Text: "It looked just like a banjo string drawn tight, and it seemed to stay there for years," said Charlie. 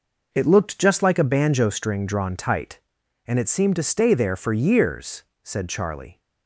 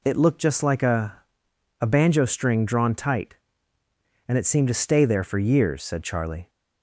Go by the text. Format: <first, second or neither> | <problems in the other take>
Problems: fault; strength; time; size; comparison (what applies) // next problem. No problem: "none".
first | says "a" twice; at 1.7 s